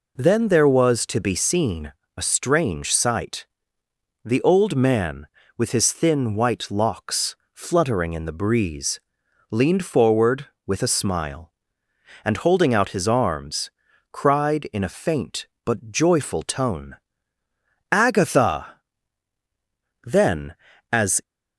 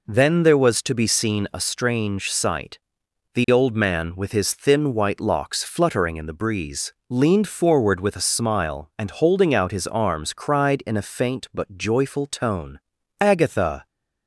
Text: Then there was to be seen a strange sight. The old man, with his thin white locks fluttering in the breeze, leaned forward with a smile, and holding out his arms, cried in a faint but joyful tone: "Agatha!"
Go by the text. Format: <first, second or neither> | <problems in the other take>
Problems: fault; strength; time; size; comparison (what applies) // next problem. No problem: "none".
second | pauses between "seen" and "a"; slight; at 1.9 s; 0.24 s long // pauses between "locks" and "fluttering"; slight; at 7.3 s; 0.18 s long // goes on to say "Then as"; noticeable; from 20.0 s on; 1.1 s long